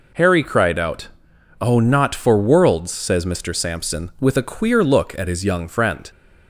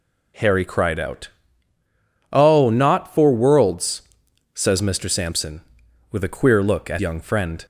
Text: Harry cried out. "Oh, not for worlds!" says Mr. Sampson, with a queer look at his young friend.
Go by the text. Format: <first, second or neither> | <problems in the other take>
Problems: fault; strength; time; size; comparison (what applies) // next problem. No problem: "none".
first | skips "his"; at 7.0 s